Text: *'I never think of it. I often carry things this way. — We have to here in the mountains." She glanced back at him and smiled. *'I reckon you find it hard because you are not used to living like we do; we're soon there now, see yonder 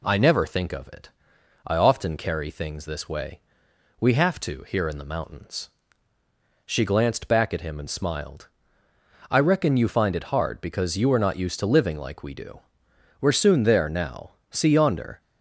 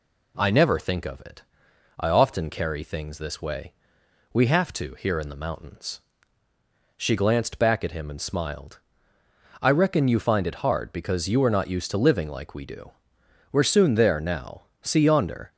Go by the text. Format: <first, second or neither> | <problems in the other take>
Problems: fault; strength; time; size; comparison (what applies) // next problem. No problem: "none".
neither | none